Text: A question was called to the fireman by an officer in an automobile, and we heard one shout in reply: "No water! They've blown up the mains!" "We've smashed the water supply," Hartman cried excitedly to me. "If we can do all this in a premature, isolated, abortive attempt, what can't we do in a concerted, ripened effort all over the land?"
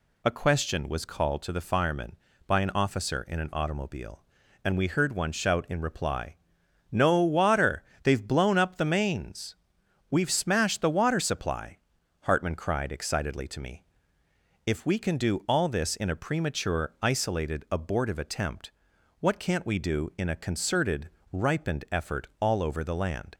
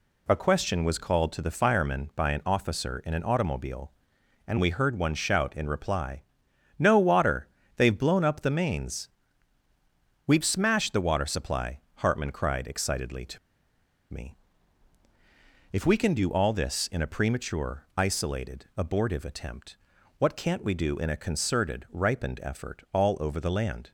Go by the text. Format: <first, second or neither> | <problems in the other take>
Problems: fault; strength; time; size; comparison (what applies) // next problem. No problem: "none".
first | pauses between "to" and "me"; noticeable; at 13.3 s; 0.74 s long